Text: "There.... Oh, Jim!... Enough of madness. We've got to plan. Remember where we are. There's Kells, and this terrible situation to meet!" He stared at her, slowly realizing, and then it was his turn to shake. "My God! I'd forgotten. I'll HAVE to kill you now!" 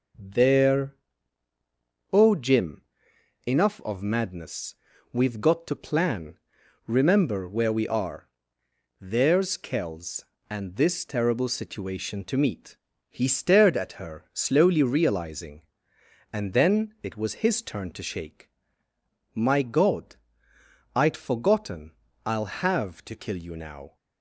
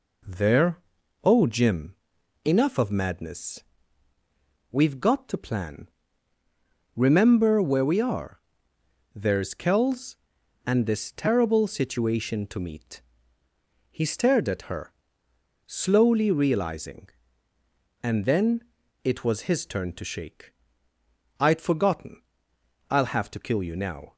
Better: first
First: none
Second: pauses between "then" and "it"; at 18.6 s; 0.42 s long // skips "My God"; at 20.9 s

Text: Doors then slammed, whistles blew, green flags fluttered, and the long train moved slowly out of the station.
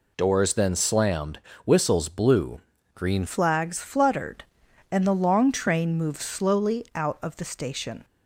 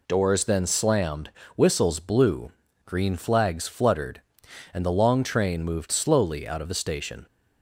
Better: second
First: changes voice at "flags"; from 3.2 s on; 4.8 s long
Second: none

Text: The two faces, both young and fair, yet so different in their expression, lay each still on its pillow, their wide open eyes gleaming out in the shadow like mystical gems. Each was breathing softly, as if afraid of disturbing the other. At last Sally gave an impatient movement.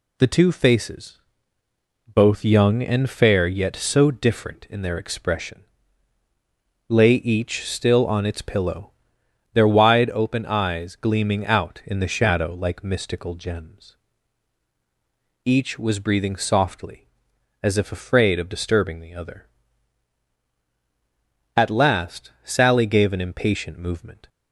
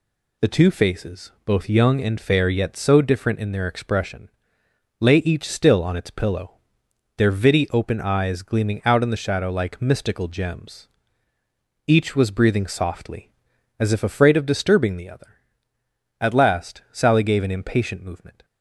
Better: first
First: none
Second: says "vitty" for "wide"; at 7.3 s

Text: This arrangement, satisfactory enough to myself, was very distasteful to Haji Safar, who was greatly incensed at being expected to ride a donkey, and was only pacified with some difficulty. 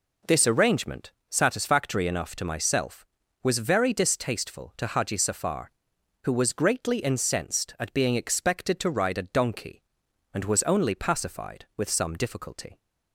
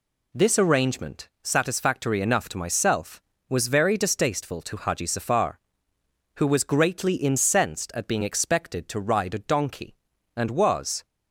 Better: first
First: none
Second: stops before "only pacified with some difficulty"; at 11.0 s

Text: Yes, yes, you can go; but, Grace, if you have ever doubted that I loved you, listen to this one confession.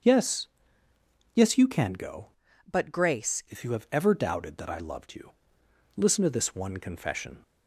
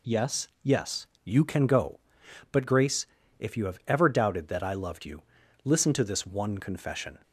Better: second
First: starts louder than the rest; until 1.9 s; 7 dB // changes voice from "but" to "Grace"; from 2.7 to 3.4 s; 0.7 s long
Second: none

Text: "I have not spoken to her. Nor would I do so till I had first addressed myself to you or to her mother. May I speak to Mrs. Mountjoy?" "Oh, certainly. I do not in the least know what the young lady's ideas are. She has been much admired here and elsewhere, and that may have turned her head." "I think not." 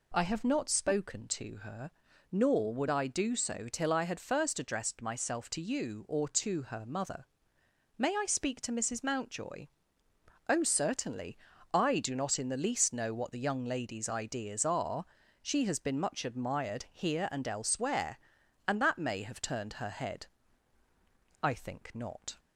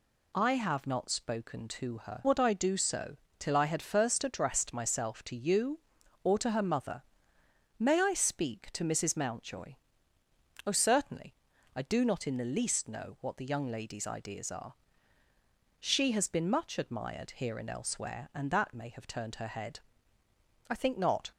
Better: first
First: none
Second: skips "Nor"; at 2.2 s // pauses between "so" and "till"; slight; at 3.1 s; 0.22 s long

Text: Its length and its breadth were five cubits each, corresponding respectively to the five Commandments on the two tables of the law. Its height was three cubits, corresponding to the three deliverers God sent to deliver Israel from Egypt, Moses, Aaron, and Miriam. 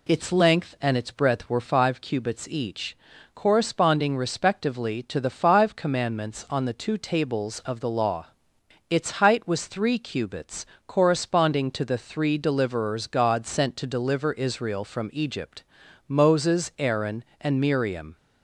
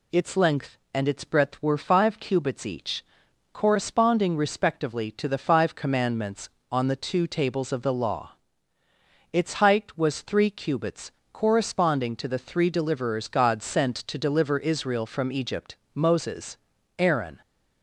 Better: first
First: none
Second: stops before "and Miriam"; at 17.4 s

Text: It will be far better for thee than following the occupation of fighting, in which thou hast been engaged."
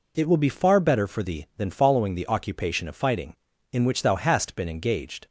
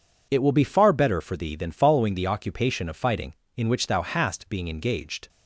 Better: first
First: none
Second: says "being" for "been"; at 4.5 s

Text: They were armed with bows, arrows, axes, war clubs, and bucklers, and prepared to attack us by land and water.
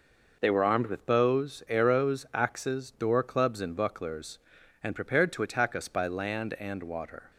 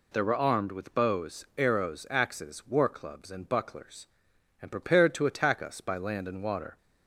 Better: second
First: says "door" for "war"; at 2.9 s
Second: none

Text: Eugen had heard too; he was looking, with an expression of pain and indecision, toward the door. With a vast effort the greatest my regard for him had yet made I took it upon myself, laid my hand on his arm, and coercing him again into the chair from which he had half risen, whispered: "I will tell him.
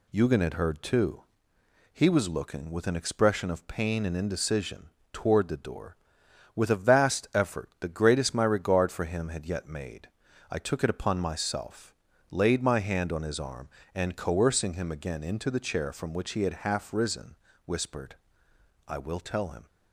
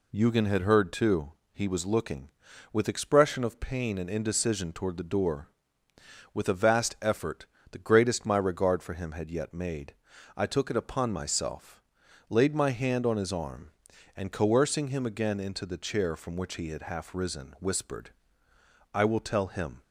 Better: first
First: pauses between "made" and "I"; at 10.0 s; 0.42 s long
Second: skips "an"; at 2.8 s // pauses between "effort" and "the"; slight; at 7.4 s; 0.24 s long // pauses between "made" and "I"; at 9.9 s; 0.42 s long

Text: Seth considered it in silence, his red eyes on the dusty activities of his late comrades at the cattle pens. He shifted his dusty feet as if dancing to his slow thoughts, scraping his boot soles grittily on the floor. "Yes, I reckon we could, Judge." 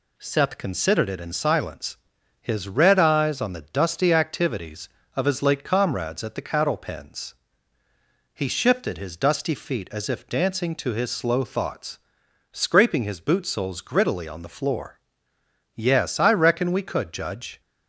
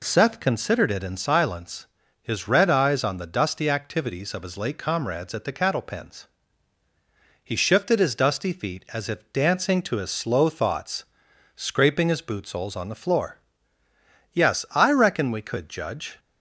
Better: first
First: none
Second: skips "grittily"; at 12.7 s

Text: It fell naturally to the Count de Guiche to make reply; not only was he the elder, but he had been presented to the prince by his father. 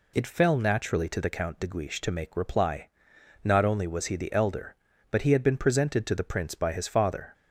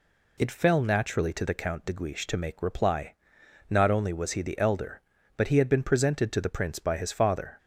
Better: neither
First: none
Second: none

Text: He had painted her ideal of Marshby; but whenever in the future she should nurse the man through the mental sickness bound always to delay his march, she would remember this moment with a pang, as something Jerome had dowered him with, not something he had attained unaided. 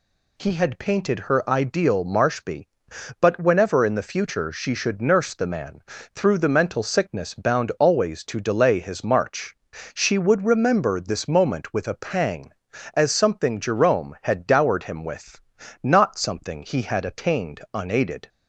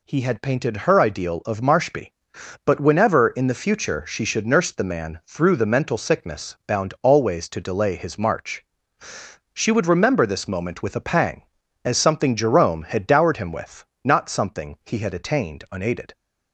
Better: second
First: skips "of"; at 2.0 s // pauses between "man" and "through"; slight; at 5.8 s; 0.32 s long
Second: none

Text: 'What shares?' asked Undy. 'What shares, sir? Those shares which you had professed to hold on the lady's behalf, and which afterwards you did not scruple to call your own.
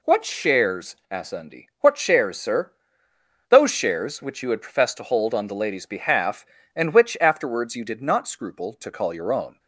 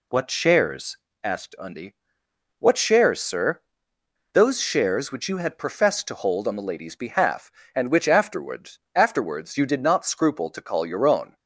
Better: first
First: none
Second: says "afterwards" twice; at 8.9 s

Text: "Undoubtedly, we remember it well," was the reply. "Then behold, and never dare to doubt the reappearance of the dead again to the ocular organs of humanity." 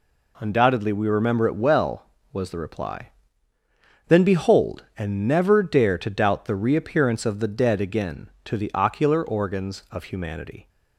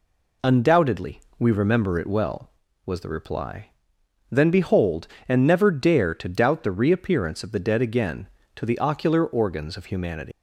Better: first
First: none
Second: leaves "humanity" unfinished; at 10.3 s; 200 ms

